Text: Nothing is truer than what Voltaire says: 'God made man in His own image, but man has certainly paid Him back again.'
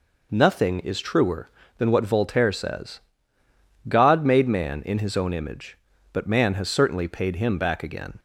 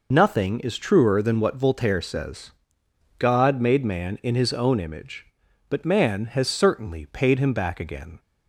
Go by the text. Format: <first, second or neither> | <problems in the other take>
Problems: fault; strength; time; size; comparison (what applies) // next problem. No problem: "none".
first | loses the start of "Nothing"; at 0.1 s; 50 ms